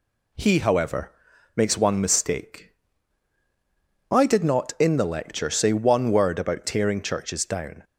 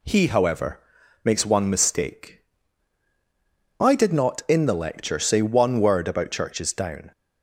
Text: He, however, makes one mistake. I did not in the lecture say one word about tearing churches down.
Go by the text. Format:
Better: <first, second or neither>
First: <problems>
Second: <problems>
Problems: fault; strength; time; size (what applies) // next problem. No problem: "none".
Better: first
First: none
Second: skips "tearing"; at 6.3 s